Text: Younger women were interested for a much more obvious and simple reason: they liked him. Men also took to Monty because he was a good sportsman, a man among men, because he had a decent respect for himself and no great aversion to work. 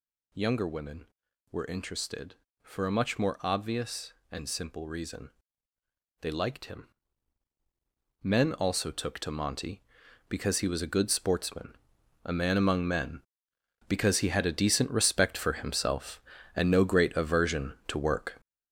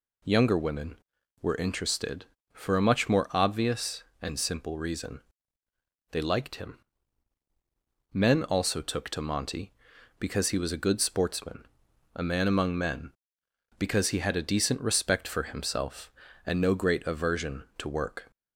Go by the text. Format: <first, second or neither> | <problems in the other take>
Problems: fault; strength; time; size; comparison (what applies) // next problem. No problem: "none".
second | gets louder; strong; throughout; 8 dB